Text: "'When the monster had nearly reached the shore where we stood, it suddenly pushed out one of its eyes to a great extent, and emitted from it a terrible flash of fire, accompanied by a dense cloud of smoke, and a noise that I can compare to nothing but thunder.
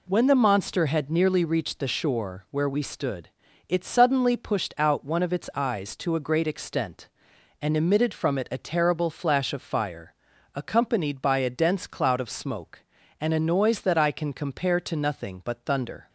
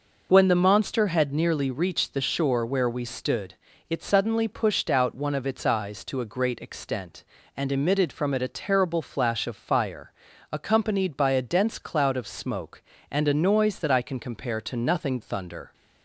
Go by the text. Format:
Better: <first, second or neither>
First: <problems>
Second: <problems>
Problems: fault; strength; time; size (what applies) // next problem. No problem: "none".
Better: first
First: none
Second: skips "but"; at 15.2 s